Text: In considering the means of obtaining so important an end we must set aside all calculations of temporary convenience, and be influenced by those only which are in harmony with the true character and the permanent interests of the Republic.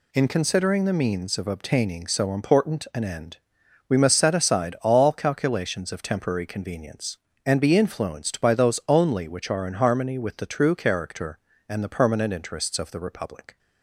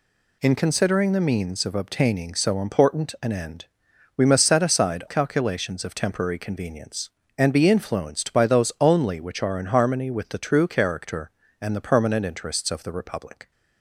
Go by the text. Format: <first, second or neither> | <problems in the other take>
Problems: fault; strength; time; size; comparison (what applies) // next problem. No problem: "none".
first | pauses between "end" and "we"; noticeable; at 3.6 s; 0.54 s long; noticeable in the first // skips "all"; at 5.0 s